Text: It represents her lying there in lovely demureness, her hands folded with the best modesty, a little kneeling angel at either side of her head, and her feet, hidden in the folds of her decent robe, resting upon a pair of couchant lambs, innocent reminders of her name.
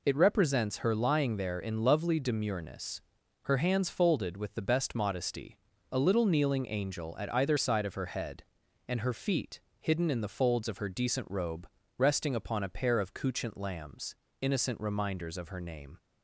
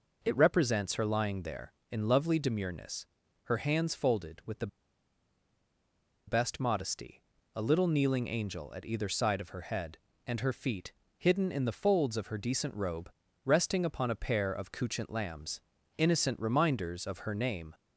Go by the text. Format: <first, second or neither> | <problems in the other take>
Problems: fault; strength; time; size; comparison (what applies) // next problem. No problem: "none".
first | pauses between "the" and "best"; strong; at 4.6 s; 1.5 s long